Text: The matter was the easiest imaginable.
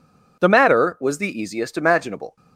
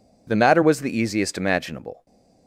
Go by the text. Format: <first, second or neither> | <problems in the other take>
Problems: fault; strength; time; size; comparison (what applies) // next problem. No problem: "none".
neither | none